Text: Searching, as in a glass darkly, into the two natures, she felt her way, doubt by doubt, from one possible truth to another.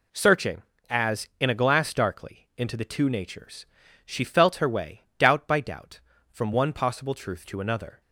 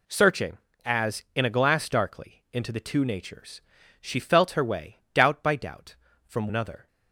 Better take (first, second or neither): first